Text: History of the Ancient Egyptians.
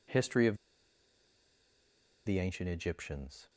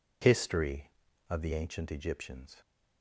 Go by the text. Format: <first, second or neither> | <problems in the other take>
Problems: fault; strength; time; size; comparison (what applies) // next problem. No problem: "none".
second | pauses between "of" and "the"; strong; at 0.5 s; 1.6 s long